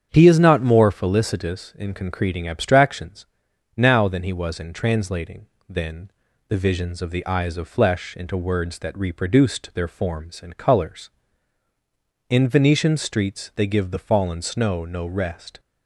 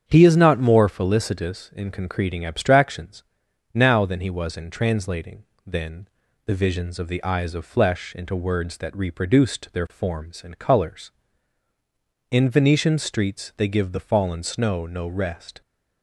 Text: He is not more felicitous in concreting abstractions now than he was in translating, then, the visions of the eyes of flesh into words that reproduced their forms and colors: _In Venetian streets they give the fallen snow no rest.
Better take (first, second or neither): neither